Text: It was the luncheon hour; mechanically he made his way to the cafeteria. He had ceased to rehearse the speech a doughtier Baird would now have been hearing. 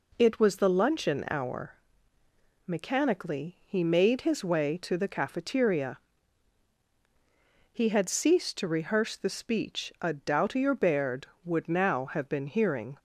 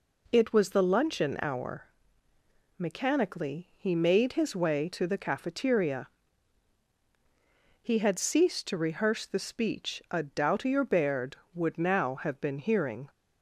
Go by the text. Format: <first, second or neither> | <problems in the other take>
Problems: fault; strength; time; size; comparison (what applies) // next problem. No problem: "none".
neither | none